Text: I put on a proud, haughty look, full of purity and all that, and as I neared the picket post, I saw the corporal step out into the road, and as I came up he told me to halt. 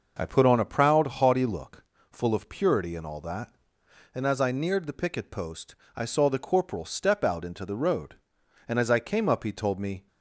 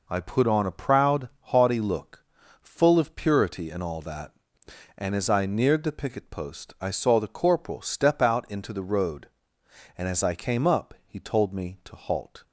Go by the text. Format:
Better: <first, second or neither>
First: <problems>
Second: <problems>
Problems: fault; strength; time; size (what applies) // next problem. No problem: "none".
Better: second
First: stops before "to halt"; at 10.0 s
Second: none